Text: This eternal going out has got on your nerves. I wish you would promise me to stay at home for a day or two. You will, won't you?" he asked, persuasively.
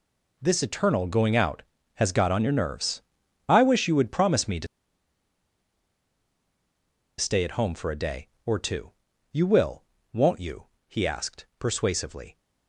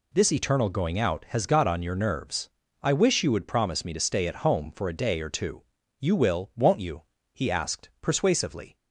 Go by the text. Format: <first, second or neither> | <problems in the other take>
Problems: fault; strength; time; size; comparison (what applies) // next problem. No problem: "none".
second | pauses between "to" and "stay"; strong; at 4.6 s; 2.5 s long